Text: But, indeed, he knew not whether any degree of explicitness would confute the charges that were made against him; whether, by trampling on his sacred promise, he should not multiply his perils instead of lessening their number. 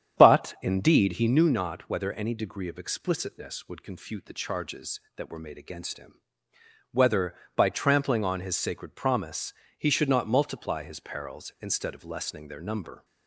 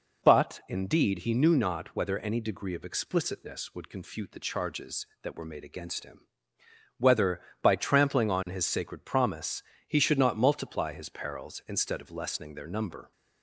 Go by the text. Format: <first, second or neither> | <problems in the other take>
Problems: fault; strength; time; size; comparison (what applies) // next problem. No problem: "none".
second | starts louder than the rest; strong; until 1.5 s; 9 dB